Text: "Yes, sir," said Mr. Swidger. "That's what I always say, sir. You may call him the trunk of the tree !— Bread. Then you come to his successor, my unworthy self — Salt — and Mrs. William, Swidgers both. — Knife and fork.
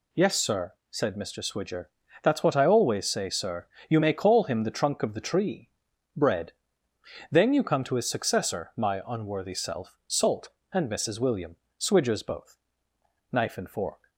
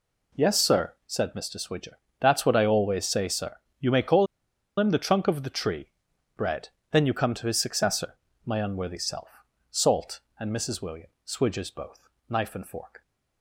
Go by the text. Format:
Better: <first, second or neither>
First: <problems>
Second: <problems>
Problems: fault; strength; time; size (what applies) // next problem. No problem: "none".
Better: first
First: none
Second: pauses between "call" and "him"; noticeable; at 4.2 s; 0.53 s long